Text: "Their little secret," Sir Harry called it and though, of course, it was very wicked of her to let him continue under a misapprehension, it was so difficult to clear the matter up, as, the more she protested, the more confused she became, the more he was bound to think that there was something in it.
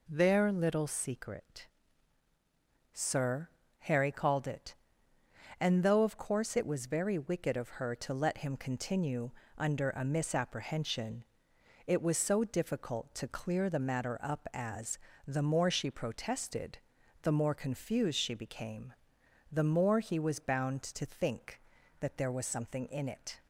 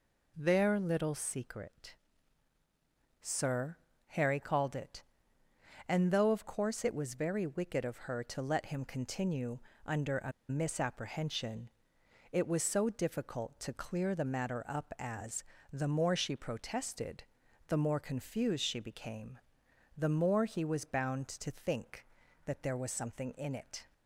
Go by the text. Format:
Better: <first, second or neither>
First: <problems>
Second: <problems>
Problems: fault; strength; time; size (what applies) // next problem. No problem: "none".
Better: first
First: pauses between "Sir" and "Harry"; slight; at 3.4 s; 0.32 s long // pauses between "continue" and "under"; slight; at 9.3 s; 0.26 s long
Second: pauses between "Sir" and "Harry"; slight; at 3.7 s; 0.32 s long // pauses between "continue" and "under"; slight; at 9.5 s; 0.26 s long // pauses between "a" and "misapprehension"; slight; at 10.3 s; 0.18 s long